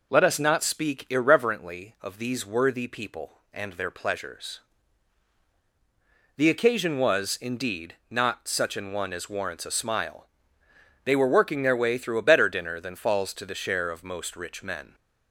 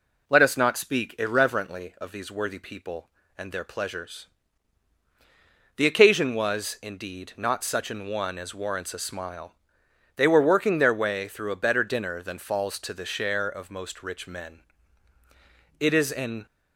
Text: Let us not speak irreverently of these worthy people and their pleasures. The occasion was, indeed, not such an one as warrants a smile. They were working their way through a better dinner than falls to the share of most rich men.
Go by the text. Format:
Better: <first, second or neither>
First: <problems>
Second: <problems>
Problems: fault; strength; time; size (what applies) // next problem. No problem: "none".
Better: first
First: none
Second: goes on to say "It is an"; noticeable; from 15.7 s on; 0.66 s long